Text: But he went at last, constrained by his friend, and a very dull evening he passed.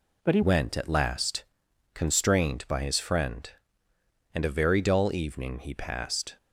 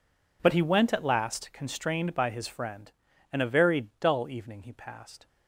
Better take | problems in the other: second | changes voice at "went"; from 0.4 s on; 5.9 s long

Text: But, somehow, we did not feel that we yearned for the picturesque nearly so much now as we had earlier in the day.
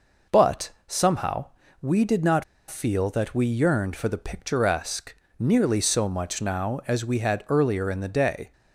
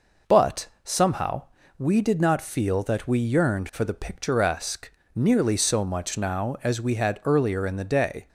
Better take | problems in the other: second | pauses between "not" and "feel"; slight; at 2.4 s; 0.24 s long // pauses between "picturesque" and "nearly"; slight; at 5.1 s; 0.24 s long; slight in the second

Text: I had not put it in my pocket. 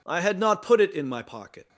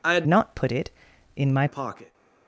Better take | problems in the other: first | changes voice from "not" to "my"; from 0.2 to 1.6 s; 1.4 s long

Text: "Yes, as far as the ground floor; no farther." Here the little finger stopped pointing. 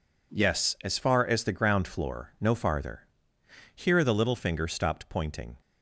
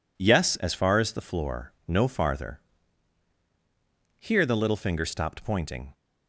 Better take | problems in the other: first | skips "ground"; at 1.1 s

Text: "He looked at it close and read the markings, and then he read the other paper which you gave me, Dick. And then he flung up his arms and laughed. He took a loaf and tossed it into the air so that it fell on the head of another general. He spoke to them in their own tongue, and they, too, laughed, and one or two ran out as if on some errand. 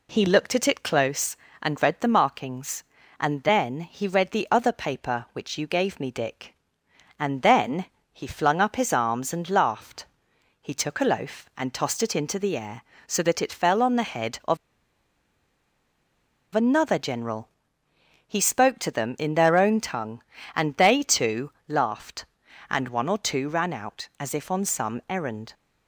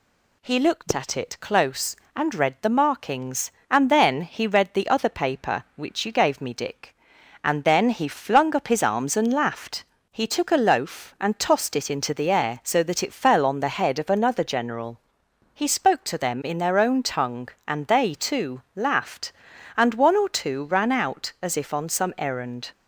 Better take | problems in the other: second | pauses between "then" and "he"; slight; at 7.8 s; 0.26 s long // pauses between "of" and "another"; strong; at 14.5 s; 1.9 s long

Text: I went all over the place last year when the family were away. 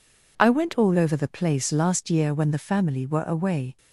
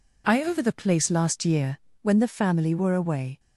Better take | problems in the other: first | skips "went all"; at 0.4 s // pauses between "year" and "when"; slight; at 1.7 s; 0.24 s long

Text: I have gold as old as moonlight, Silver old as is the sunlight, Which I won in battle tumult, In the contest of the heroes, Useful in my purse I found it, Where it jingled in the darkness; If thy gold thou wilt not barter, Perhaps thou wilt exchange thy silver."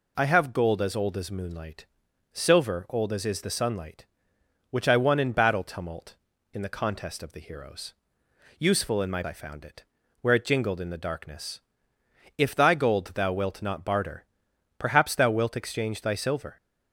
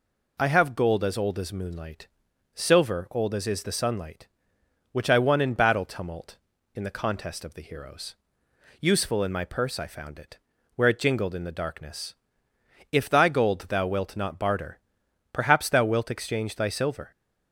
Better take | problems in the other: second | skips "purse"; at 9.2 s

